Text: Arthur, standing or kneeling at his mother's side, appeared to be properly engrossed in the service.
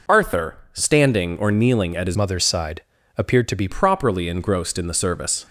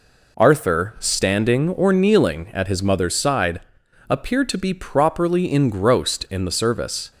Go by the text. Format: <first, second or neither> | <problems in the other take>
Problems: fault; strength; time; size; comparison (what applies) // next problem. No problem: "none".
second | changes voice from "mother's" to "be"; from 2.1 to 3.6 s; 1.5 s long